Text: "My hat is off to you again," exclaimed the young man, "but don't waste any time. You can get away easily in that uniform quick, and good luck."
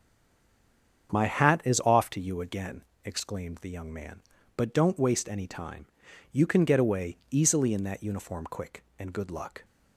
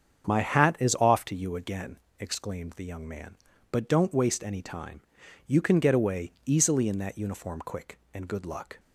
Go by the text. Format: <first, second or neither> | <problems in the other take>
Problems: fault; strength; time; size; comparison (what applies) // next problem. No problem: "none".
second | stays silent before the first word; until 1.0 s; 1.0 s long // starts louder than the rest; strong; until 2.1 s; 7.5 dB; strong in the second